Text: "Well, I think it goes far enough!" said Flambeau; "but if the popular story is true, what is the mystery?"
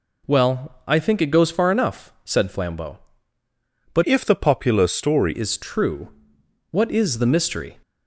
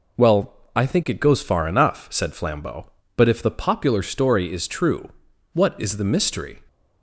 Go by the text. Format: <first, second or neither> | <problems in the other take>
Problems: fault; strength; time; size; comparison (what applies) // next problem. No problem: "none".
second | changes voice from "if" to "story"; from 4.0 to 5.3 s; 1.3 s long